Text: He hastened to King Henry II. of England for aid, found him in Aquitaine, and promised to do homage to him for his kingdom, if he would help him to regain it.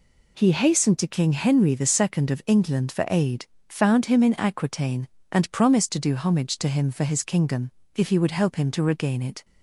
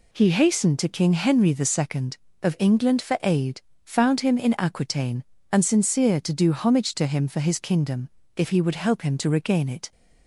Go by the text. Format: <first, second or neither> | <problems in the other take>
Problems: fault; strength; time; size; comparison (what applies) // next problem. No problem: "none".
first | says "sincere" for "promised"; at 5.6 s